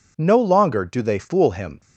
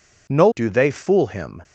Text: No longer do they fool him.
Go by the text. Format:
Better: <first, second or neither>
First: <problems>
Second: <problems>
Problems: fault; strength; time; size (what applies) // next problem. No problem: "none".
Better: first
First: none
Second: skips "longer"; at 0.4 s